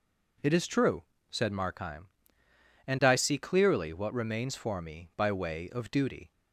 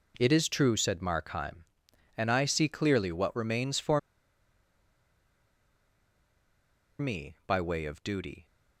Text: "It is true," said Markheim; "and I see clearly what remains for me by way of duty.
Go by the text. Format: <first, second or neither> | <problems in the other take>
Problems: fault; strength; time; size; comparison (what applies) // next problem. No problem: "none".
first | pauses between "for" and "me"; strong; at 3.9 s; 2.9 s long